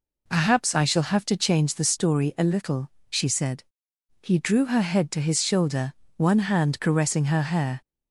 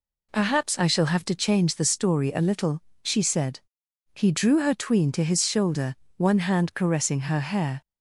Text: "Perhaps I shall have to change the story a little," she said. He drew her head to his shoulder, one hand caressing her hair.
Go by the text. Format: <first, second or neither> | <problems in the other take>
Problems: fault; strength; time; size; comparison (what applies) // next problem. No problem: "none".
first | says "tween" for "head"; at 4.7 s